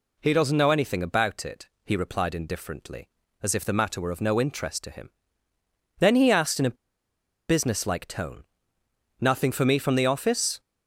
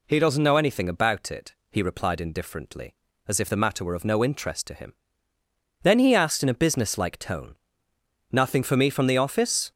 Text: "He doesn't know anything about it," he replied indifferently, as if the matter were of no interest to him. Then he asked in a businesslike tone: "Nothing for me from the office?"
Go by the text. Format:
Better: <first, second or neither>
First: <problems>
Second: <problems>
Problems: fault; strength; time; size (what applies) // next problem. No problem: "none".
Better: second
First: pauses between "a" and "businesslike"; noticeable; at 6.7 s; 0.75 s long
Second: none